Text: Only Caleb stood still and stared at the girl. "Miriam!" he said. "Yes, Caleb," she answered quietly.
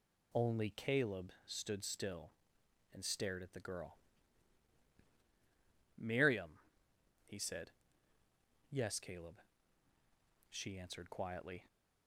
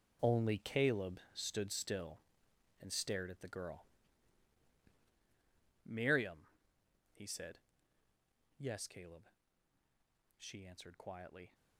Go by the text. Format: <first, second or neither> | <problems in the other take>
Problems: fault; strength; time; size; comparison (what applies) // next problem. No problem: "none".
first | gets quieter; strong; throughout; 13.5 dB